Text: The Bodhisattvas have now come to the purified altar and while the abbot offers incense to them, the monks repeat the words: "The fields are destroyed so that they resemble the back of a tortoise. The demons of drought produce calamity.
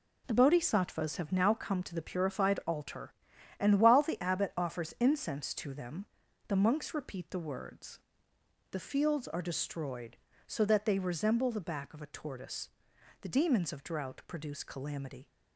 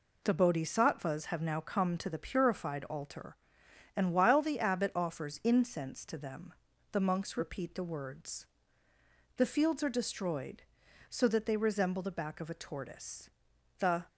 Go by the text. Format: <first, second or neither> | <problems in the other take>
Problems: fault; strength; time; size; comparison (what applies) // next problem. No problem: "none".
first | stops before "demons of drought produce calamity"; at 14.0 s